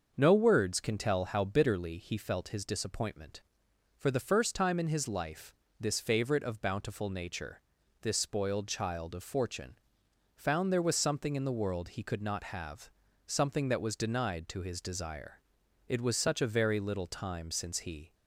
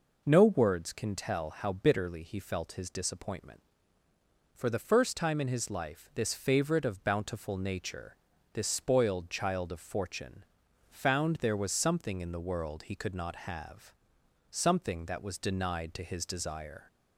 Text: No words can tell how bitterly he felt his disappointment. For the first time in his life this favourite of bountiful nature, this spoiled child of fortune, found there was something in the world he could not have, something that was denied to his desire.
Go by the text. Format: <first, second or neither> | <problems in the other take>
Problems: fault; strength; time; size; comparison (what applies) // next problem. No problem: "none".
second | starts louder than the rest; until 1.1 s; 6.5 dB // pauses between "life" and "this"; slight; at 5.5 s; 0.24 s long // goes on to say "It was such a very little time since he"; strong; from 15.8 s on; 2.2 s long